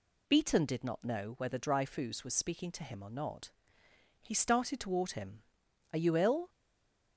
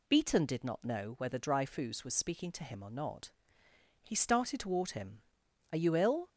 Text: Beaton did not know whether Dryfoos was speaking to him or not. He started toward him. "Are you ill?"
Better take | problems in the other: second | stays silent after the last word; slight; from 6.4 s on; 0.7 s long

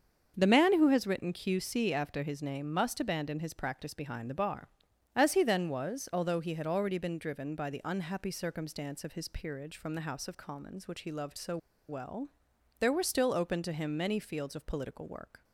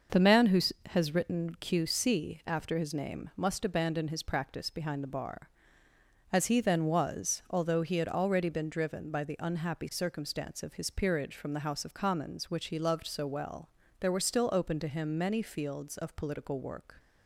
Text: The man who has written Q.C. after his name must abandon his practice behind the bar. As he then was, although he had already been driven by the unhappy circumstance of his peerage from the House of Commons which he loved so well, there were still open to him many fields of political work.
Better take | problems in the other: second | starts louder than the rest; until 1.3 s; 6.5 dB // pauses between "so" and "well"; slight; at 11.5 s; 0.31 s long

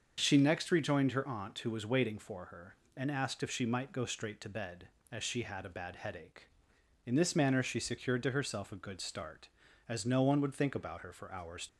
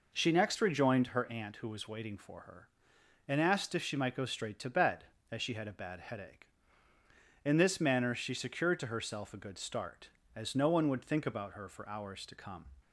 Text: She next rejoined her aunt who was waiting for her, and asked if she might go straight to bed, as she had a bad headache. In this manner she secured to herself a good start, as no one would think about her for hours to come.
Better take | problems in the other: second | starts louder than the rest; until 1.2 s; 6.5 dB // stops before "to come"; at 11.6 s

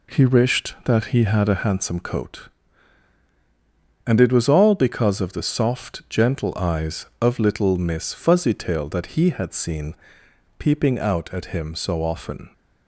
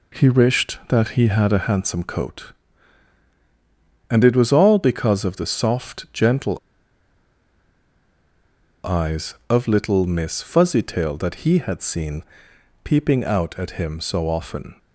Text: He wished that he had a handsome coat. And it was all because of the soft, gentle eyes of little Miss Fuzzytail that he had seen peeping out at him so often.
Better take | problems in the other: first | pauses between "gentle" and "eyes"; strong; at 6.5 s; 2.2 s long // pauses between "seen" and "peeping"; noticeable; at 12.2 s; 0.62 s long; noticeable in the first

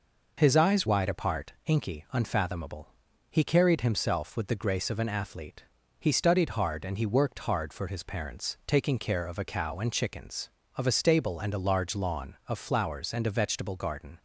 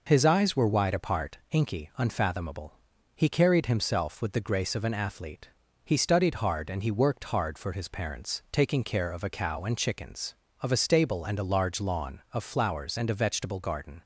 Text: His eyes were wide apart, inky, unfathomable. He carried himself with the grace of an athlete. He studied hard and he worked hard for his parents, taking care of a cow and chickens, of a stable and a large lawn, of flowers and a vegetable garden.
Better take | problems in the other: second | skips "were"; at 0.8 s

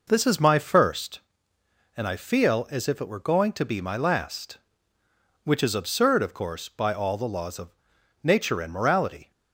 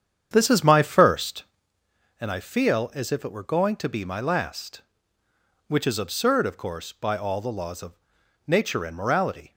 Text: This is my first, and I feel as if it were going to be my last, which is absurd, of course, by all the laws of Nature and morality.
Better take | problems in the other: first | starts louder than the rest; strong; until 1.8 s; 8.5 dB // pauses between "of" and "Nature"; noticeable; at 7.9 s; 0.54 s long; noticeable in the first

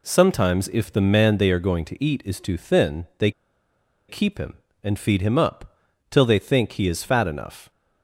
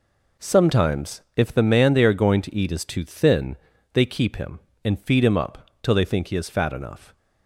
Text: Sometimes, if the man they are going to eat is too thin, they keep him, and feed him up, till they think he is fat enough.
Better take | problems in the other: second | pauses between "they" and "keep"; noticeable; at 3.3 s; 0.77 s long

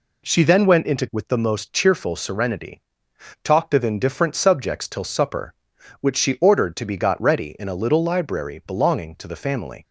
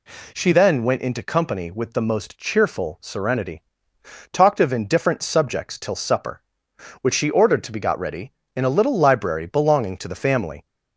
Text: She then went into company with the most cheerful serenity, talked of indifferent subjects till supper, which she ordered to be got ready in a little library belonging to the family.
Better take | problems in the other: second | skips "company"; at 1.0 s

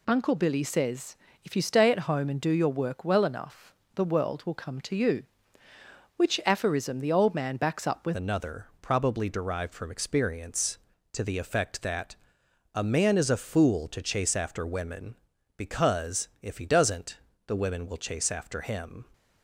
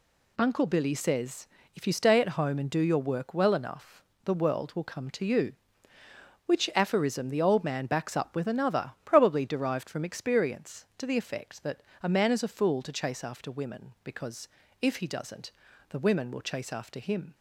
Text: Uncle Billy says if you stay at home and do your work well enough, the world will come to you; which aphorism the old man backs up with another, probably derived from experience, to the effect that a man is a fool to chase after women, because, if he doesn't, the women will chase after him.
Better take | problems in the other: second | pauses between "says" and "if"; slight; at 1.1 s; 0.30 s long; slight in the second // changes voice at "another"; from 8.1 s on; 10.9 s long // pauses between "that" and "a"; noticeable; at 12.1 s; 0.56 s long; slight in the second

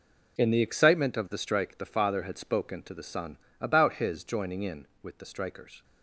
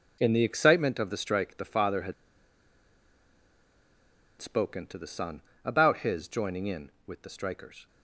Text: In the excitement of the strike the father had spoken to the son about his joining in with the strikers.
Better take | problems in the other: first | pauses between "had" and "spoken"; strong; at 2.1 s; 2.2 s long // pauses between "son" and "about"; slight; at 5.4 s; 0.22 s long; slight in the first

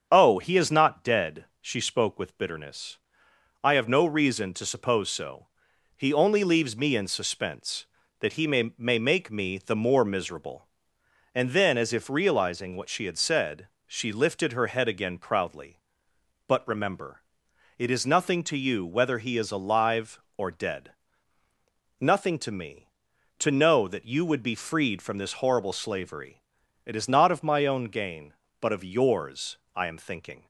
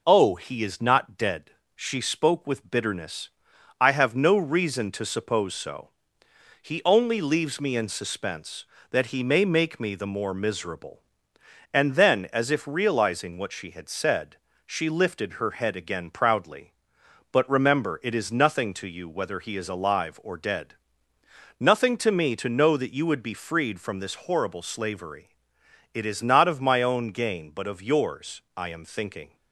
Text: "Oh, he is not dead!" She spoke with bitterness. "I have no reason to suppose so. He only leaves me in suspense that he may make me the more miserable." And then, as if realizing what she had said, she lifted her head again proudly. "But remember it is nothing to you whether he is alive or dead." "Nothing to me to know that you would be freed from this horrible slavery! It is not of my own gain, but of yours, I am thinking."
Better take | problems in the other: second | starts louder than the rest; strong; until 1.1 s; 7 dB // says "may" twice; at 8.7 s // pauses between "remember" and "it"; noticeable; at 17.2 s; 0.54 s long

